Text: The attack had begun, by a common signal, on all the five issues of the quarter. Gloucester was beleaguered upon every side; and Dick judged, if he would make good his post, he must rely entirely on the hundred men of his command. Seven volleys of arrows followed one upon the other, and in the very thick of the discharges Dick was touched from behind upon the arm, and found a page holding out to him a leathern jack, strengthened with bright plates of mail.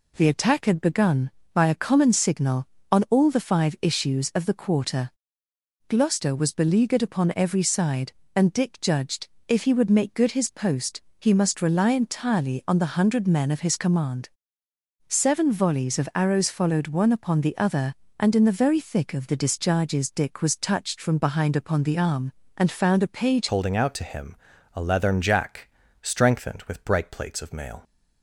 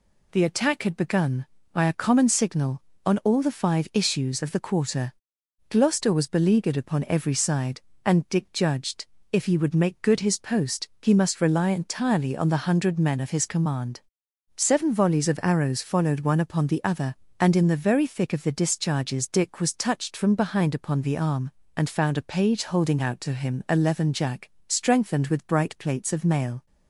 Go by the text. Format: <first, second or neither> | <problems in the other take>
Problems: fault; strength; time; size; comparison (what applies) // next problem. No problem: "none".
second | changes voice at "holding"; from 23.4 s on; 4.4 s long // pauses between "him" and "a"; at 24.3 s; 0.40 s long